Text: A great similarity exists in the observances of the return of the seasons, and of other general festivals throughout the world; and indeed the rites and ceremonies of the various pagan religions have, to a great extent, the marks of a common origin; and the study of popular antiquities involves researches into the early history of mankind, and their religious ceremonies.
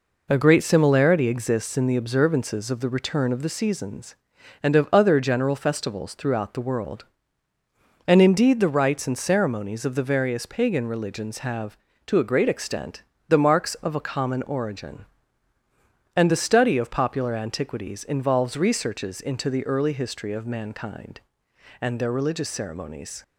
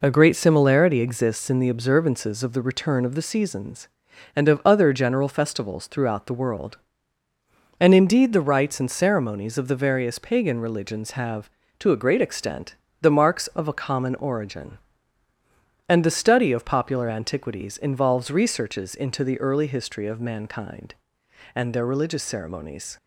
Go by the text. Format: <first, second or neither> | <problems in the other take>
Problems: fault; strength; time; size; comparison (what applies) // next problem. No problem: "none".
neither | none